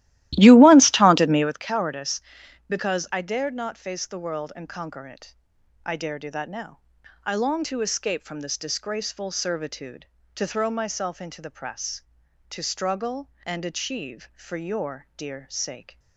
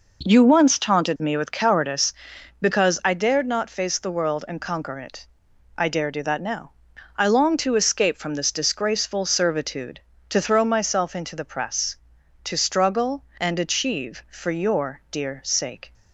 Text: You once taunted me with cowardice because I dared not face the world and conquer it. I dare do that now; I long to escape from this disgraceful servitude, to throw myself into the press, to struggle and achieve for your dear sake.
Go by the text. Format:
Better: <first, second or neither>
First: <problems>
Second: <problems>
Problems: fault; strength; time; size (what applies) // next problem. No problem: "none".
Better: second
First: starts louder than the rest; strong; until 1.6 s; 15.5 dB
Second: none